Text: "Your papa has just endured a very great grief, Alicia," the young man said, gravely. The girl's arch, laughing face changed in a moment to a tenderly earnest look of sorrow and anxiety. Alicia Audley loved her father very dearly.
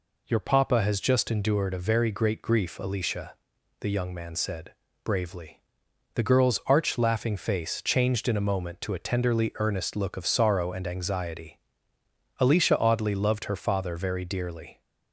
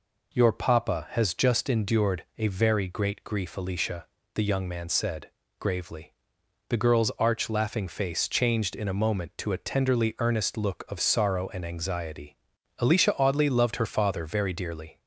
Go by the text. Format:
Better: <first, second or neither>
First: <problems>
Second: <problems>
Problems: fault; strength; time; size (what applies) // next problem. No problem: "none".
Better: second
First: says "bravely" for "gravely"; at 5.0 s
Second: none